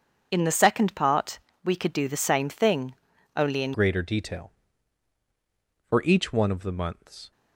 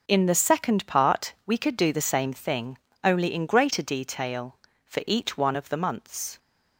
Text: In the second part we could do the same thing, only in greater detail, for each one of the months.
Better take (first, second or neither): second